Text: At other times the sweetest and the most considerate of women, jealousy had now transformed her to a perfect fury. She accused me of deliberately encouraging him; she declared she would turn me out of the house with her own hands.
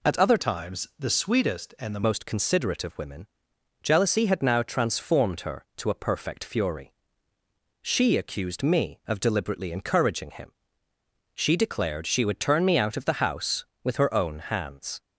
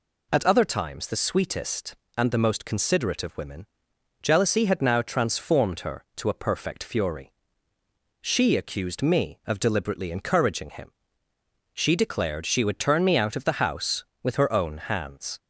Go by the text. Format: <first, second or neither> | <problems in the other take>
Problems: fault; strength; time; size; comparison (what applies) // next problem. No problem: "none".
second | changes voice from "times" to "the"; from 0.3 to 2.0 s; 1.7 s long